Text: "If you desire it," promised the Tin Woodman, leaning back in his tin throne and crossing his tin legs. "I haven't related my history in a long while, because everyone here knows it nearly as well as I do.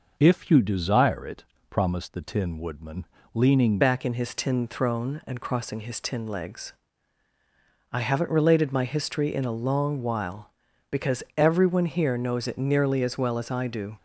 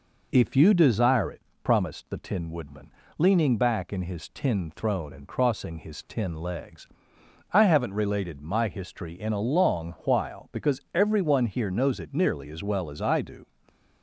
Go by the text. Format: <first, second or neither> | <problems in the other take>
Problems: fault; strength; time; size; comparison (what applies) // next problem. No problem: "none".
second | changes voice at "back"; from 3.8 s on; 10.1 s long